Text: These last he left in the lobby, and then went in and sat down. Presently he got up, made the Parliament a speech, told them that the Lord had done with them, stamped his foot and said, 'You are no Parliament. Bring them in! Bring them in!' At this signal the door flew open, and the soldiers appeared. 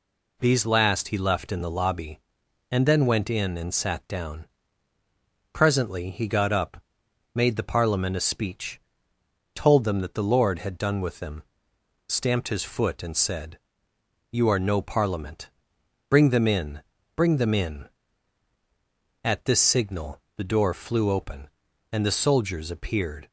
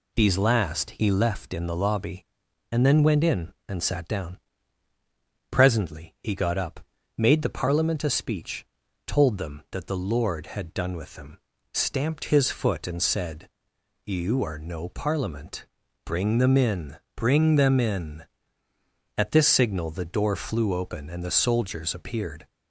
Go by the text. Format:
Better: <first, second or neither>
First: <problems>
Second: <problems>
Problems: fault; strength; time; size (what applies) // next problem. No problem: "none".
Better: neither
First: none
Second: none